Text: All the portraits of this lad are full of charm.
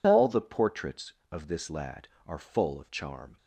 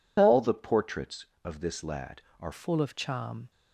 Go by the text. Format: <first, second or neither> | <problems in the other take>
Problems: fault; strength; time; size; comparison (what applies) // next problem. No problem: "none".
first | changes voice at "full"; from 2.5 s on; 1.0 s long